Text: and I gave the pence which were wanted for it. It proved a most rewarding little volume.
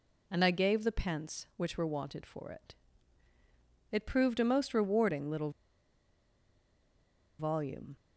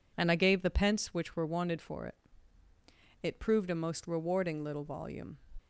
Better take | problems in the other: second | pauses between "little" and "volume"; strong; at 5.5 s; 1.8 s long

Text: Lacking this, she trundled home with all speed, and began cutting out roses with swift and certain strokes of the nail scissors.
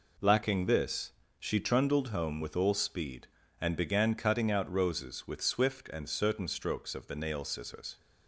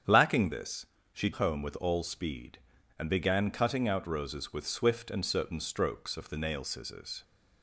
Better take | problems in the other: first | starts louder than the rest; strong; until 1.3 s; 8 dB // skips "trundled"; at 1.3 s

